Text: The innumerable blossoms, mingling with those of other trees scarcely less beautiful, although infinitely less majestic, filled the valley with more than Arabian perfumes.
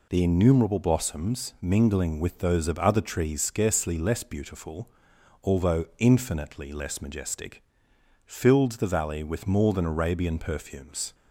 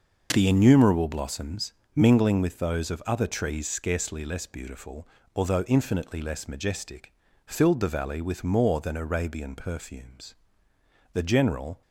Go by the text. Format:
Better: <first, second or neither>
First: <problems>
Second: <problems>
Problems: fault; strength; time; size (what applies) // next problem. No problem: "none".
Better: first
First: none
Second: starts louder than the rest; noticeable; until 1.3 s; 6 dB // goes on to say "The general"; noticeable; from 11.1 s on; 0.70 s long